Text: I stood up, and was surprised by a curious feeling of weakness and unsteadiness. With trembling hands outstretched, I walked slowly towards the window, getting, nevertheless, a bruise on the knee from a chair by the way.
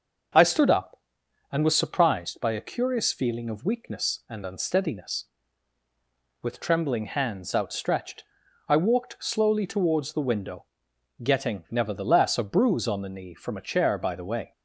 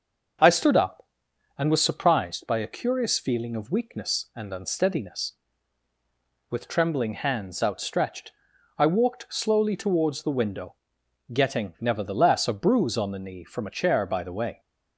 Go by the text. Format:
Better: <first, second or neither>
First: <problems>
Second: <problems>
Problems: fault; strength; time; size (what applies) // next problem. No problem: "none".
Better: neither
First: starts louder than the rest; until 1.9 s; 6 dB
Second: starts louder than the rest; until 1.9 s; 6.5 dB